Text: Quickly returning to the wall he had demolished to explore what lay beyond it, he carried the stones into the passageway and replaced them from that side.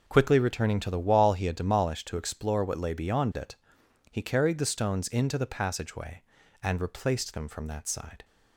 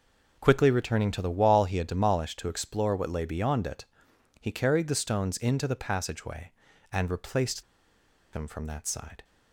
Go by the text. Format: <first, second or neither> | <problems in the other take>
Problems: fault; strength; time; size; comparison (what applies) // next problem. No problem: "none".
first | pauses between "replaced" and "them"; noticeable; at 7.6 s; 0.70 s long